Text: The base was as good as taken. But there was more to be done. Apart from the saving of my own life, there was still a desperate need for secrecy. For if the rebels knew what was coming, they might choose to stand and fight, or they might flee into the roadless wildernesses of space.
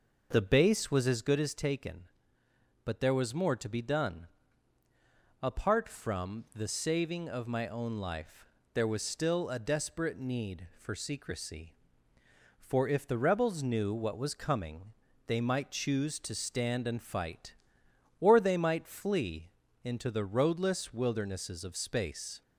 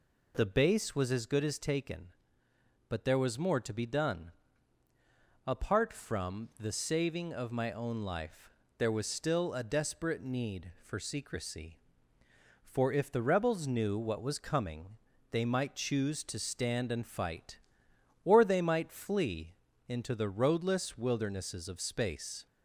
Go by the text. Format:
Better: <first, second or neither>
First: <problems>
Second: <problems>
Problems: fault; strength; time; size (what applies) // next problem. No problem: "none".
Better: second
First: starts louder than the rest; noticeable; until 1.6 s; 5.5 dB // pauses between "flee" and "into"; slight; at 19.4 s; 0.34 s long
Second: pauses between "flee" and "into"; slight; at 19.5 s; 0.34 s long